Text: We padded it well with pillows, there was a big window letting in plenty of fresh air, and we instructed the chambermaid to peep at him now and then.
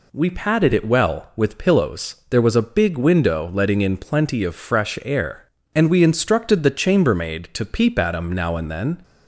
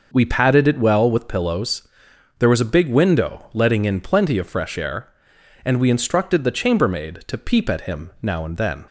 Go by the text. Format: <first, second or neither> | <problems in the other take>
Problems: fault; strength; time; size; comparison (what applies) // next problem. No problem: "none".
neither | none